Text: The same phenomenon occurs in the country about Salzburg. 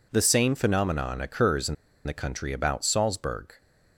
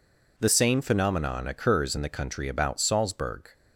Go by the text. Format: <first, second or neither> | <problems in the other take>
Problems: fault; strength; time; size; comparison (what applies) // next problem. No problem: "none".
second | pauses between "in" and "the"; slight; at 1.7 s; 0.31 s long